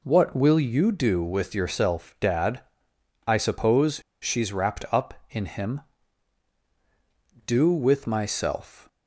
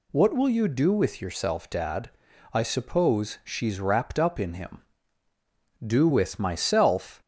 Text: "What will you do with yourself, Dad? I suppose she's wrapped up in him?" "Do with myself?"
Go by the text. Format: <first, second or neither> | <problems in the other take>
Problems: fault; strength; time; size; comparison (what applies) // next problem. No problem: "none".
second | pauses between "suppose" and "she's"; slight; at 3.9 s; 0.21 s long